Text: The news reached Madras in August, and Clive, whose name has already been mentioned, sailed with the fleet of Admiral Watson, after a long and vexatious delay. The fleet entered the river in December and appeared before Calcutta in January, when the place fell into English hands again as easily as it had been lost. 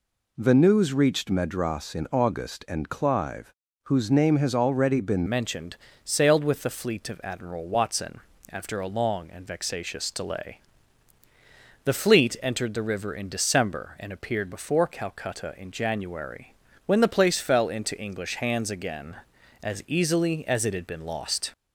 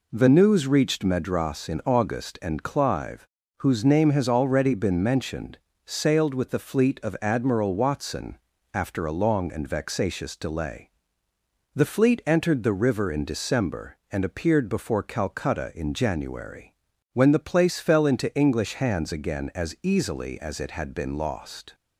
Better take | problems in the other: second | changes voice at "mentioned"; from 5.2 s on; 16.3 s long

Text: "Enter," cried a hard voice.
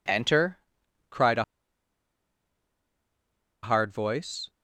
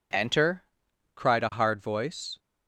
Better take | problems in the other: second | pauses between "a" and "hard"; strong; at 1.4 s; 2.2 s long

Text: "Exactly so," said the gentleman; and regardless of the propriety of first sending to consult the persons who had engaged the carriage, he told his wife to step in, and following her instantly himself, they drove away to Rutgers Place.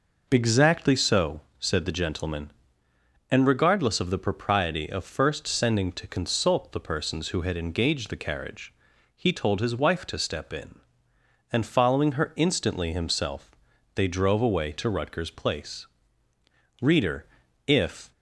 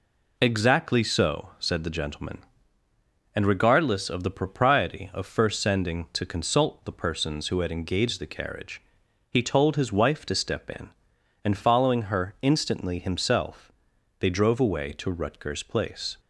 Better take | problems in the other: second | goes on to say "Reader if"; noticeable; from 16.8 s on; 1.3 s long

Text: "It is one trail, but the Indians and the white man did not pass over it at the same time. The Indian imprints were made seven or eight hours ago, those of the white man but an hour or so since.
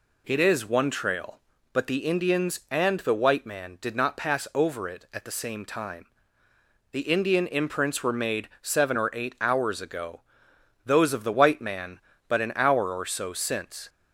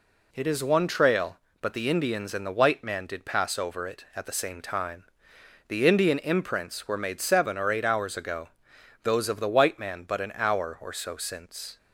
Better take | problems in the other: first | skips "not"; at 3.2 s

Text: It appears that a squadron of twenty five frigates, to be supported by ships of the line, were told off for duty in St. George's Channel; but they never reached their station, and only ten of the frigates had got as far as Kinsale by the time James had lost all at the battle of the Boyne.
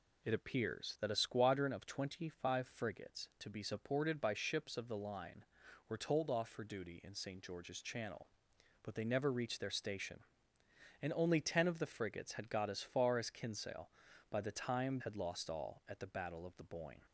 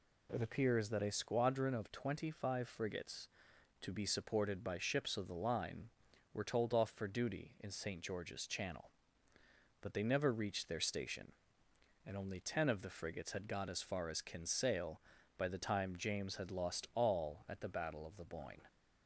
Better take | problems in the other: second | skips "James"; at 14.9 s

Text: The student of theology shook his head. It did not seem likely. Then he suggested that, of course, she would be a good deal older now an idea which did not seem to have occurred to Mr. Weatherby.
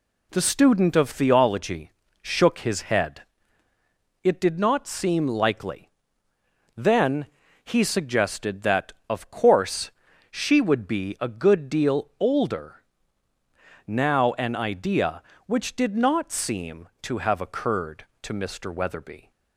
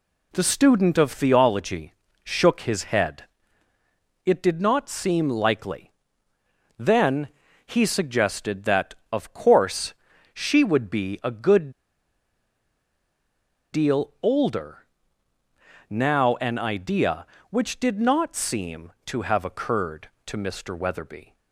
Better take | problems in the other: first | pauses between "theology" and "shook"; slight; at 1.9 s; 0.32 s long; slight in the first // pauses between "Then" and "he"; at 7.2 s; 0.38 s long; also in the first // pauses between "good" and "deal"; strong; at 11.7 s; 2.0 s long // pauses between "older" and "now"; at 14.7 s; 1.1 s long; also in the first

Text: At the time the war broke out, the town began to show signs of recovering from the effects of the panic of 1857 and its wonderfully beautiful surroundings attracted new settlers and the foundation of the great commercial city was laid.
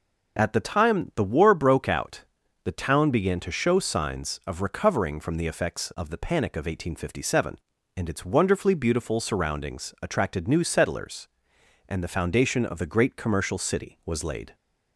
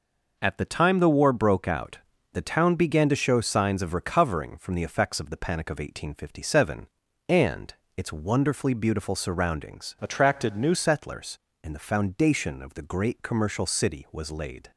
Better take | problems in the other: first | pauses between "and" and "its"; slight; at 7.7 s; 0.24 s long // changes voice from "attracted" to "new"; from 10.0 to 10.7 s; 0.7 s long

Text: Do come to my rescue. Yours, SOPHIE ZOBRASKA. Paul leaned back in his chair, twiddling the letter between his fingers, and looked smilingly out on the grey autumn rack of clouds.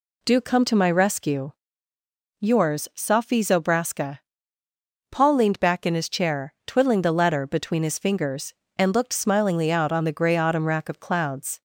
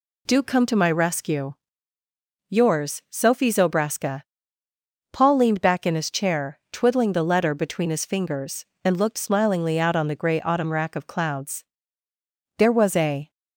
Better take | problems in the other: first | goes on to say "There was a"; noticeable; from 12.5 s on; 0.72 s long

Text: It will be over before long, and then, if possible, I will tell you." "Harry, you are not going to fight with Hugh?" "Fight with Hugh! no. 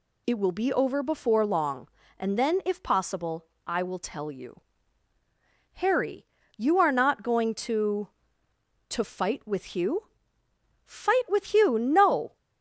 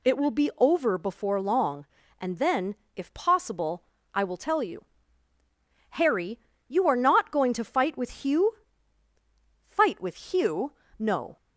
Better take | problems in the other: second | says "to" twice; at 8.8 s

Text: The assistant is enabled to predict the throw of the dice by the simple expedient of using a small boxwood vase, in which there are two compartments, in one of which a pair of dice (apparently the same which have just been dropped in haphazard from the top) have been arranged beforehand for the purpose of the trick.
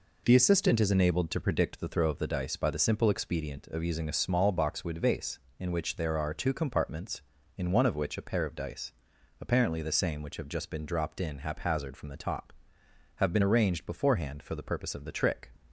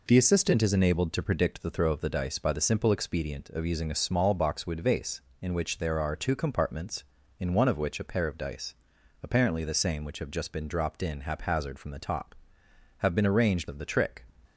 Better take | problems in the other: first | skips "beforehand for the purpose"; at 13.6 s

